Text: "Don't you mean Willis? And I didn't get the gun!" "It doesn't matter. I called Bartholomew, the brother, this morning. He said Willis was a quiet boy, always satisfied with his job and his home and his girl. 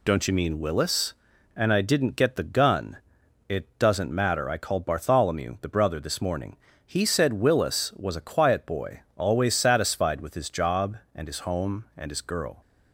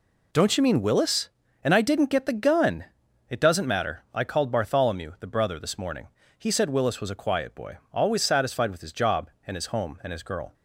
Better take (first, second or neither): neither